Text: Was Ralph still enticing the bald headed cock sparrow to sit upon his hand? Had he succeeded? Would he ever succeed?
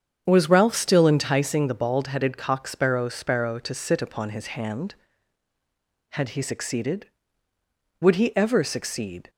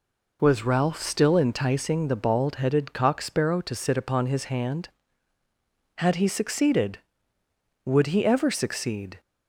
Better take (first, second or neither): second